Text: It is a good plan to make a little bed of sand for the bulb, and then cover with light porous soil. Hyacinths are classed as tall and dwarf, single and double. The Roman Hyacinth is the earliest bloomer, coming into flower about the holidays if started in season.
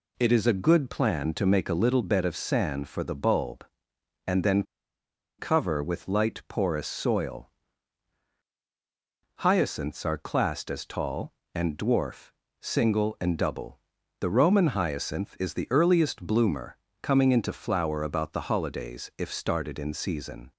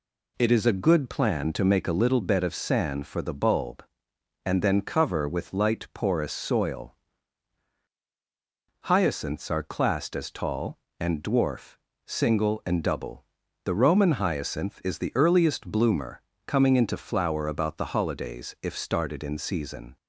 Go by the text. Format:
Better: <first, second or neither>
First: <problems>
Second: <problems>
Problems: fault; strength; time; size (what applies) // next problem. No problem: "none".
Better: second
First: pauses between "then" and "cover"; noticeable; at 4.6 s; 0.75 s long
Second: none